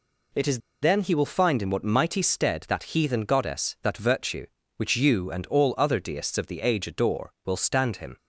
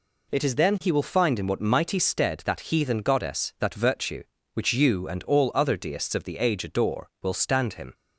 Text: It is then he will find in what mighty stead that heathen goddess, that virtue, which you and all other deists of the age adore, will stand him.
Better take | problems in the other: second | pauses between "is" and "then"; slight; at 0.5 s; 0.23 s long

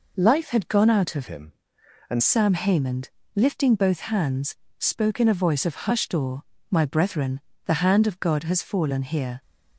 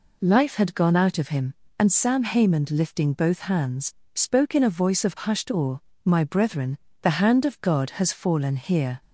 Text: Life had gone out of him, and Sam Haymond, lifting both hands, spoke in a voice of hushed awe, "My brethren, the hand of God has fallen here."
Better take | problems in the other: second | changes voice from "him" to "and"; from 1.2 to 2.2 s; 1.0 s long

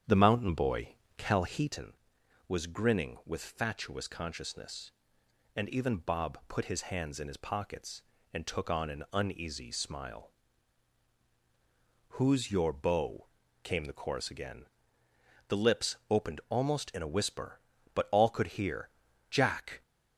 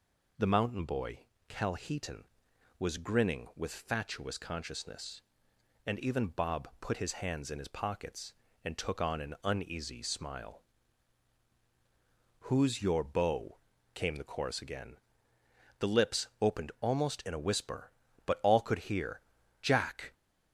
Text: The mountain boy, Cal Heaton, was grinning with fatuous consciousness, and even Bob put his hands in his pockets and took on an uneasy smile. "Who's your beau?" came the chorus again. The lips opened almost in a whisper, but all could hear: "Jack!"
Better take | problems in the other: second | starts louder than the rest; strong; until 1.8 s; 9 dB // pauses between "lips" and "opened"; slight; at 15.9 s; 0.16 s long; slight in the second

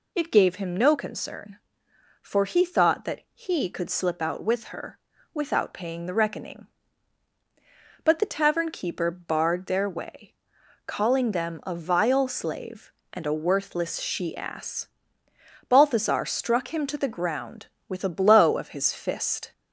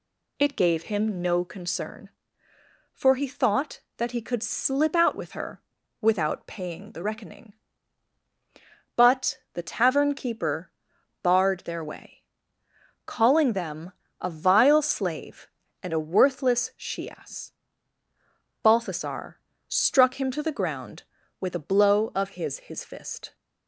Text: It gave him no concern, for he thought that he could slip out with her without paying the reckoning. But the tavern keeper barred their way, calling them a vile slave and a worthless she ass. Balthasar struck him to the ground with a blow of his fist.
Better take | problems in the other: first | pauses between "her" and "without"; at 5.6 s; 0.40 s long; slight in the first // pauses between "keeper" and "barred"; noticeable; at 10.7 s; 0.52 s long // pauses between "them" and "a"; slight; at 13.9 s; 0.28 s long // pauses between "Balthasar" and "struck"; slight; at 19.3 s; 0.30 s long // says "his" twice; at 22.5 s

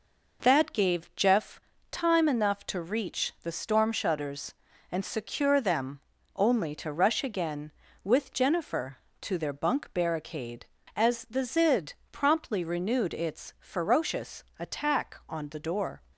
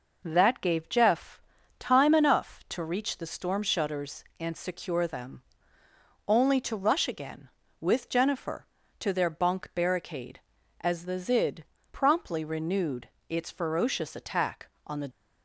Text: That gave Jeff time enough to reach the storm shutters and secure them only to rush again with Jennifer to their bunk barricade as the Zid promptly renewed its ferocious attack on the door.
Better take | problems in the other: first | pauses between "Jeff" and "time"; at 1.4 s; 0.40 s long; slight in the first // pauses between "them" and "only"; noticeable; at 5.4 s; 0.86 s long; slight in the first // pauses between "Zid" and "promptly"; slight; at 11.6 s; 0.26 s long; slight in the first // pauses between "renewed" and "its"; slight; at 13.0 s; 0.20 s long // stops before "door"; at 15.1 s

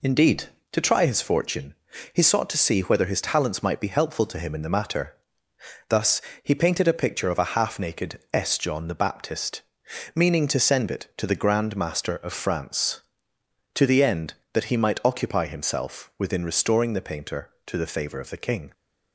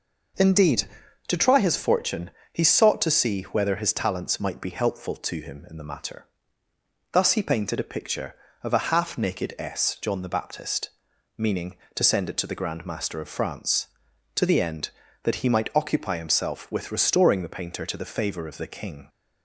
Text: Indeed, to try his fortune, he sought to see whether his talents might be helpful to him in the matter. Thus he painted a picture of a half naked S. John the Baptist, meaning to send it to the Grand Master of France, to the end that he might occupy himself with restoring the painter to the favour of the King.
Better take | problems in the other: second | pauses between "Thus" and "he"; slight; at 6.2 s; 0.22 s long // says "within" for "with"; at 16.1 s

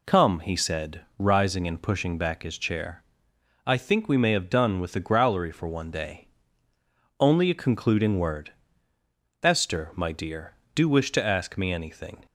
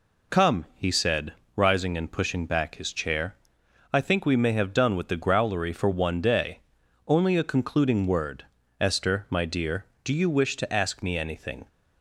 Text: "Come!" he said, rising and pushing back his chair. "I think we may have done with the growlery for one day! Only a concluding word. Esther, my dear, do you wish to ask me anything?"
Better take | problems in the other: second | skips "you"; at 10.8 s

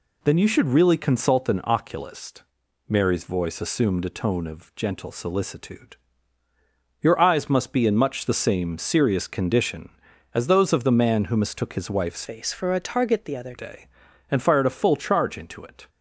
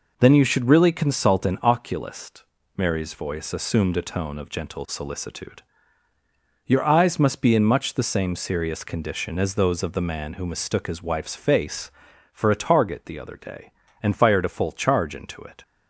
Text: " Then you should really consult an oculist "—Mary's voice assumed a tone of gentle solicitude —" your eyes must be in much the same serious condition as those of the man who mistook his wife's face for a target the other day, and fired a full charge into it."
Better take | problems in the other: second | changes voice from "face" to "other"; from 12.2 to 13.5 s; 1.3 s long

